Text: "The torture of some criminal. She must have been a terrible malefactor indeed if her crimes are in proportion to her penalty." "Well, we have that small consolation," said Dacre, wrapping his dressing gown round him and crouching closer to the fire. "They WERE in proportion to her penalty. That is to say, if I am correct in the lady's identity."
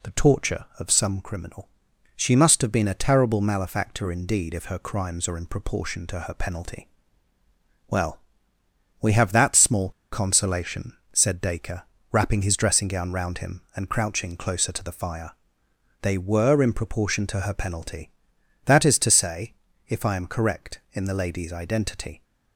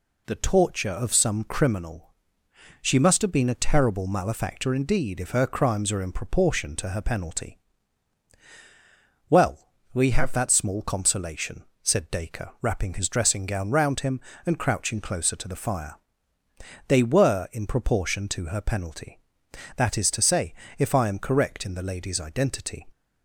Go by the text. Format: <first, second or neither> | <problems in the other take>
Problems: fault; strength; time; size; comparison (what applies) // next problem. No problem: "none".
second | pauses between "small" and "consolation"; slight; at 9.9 s; 0.21 s long